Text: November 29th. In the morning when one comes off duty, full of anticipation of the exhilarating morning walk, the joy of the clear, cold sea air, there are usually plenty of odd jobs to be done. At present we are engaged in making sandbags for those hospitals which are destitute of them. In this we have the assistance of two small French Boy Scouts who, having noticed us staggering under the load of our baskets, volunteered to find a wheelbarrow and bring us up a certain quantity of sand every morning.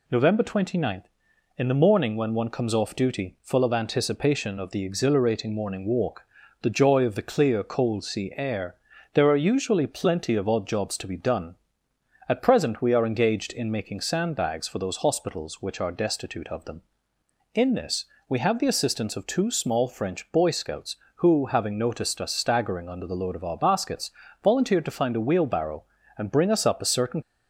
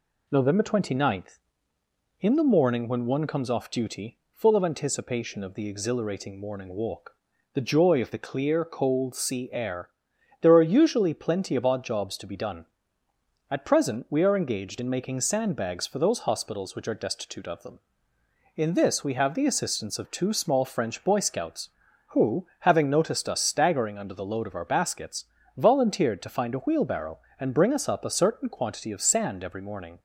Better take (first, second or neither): second